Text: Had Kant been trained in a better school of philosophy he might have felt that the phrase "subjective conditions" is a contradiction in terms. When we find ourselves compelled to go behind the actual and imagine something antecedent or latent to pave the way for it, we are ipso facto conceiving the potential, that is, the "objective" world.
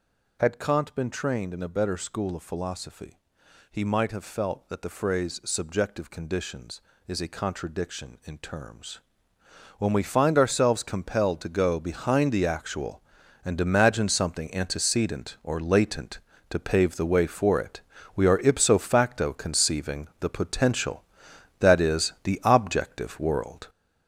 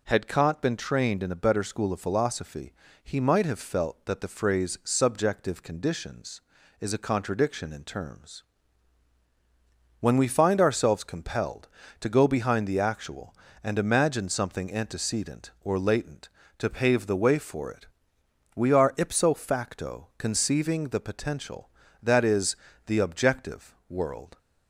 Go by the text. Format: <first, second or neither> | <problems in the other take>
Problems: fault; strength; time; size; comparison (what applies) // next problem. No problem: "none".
second | gets louder; noticeable; throughout; 6 dB // pauses between "philosophy" and "he"; noticeable; at 3.1 s; 0.54 s long; slight in the second